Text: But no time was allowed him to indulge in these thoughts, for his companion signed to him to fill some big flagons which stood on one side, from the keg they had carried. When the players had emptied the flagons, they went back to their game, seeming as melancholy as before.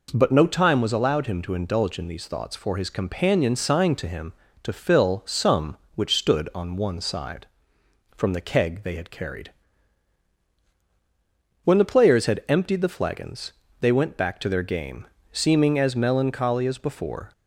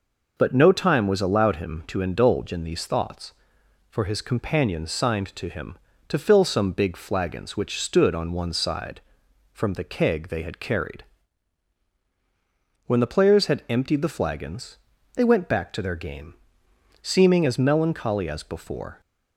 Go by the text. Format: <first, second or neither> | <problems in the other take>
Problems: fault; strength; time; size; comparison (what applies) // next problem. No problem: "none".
second | skips "big flagons"; at 5.8 s